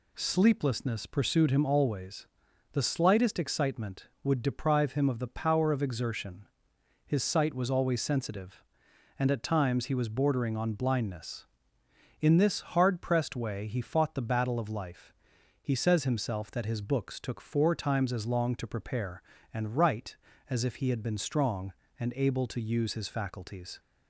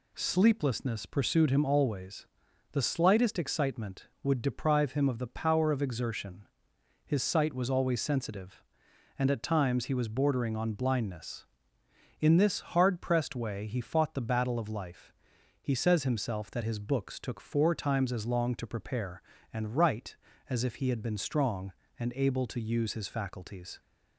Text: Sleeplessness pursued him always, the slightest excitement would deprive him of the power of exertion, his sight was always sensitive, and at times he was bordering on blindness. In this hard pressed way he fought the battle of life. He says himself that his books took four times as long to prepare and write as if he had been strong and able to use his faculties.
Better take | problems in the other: neither | none

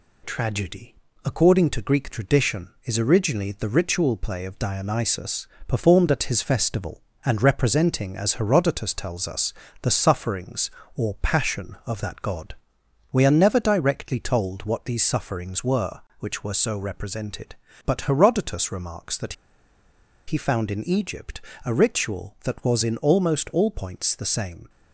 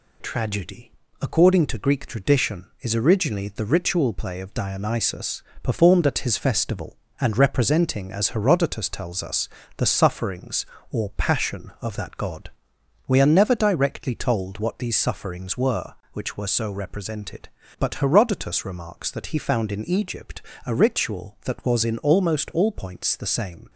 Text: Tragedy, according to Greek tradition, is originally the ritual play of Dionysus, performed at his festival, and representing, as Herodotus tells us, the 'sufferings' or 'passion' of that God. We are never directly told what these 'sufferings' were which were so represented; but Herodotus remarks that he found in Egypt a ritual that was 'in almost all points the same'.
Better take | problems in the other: second | pauses between "that" and "he"; noticeable; at 19.3 s; 0.93 s long // pauses between "Egypt" and "a"; slight; at 21.4 s; 0.24 s long; slight in the second

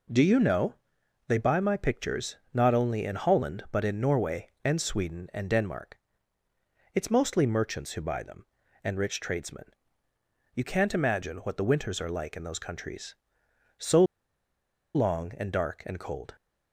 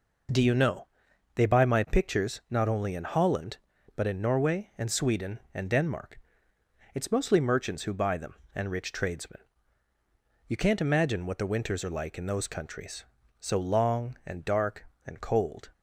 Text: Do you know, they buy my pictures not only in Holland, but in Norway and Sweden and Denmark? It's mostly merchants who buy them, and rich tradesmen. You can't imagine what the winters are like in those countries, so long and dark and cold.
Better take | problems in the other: second | pauses between "pictures" and "not"; slight; at 2.3 s; 0.18 s long // pauses between "so" and "long"; noticeable; at 14.0 s; 0.91 s long

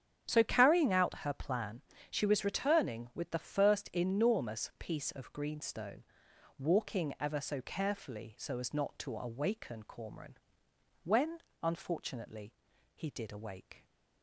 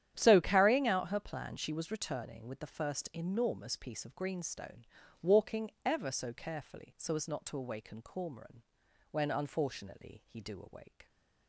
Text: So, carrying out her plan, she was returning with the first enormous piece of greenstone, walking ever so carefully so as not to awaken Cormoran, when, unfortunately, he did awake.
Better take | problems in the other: first | starts louder than the rest; strong; until 1.1 s; 10.5 dB; strong in the first // says "do" for "did"; at 10.4 s

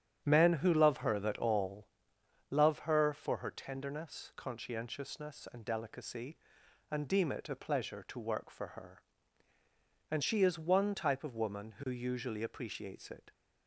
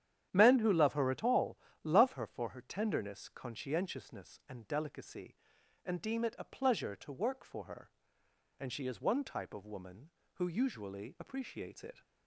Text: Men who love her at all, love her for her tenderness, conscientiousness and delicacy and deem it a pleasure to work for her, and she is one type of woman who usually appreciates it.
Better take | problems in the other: second | starts louder than the rest; strong; until 1.2 s; 9 dB; strong in the second // says "that" for "at"; at 1.1 s

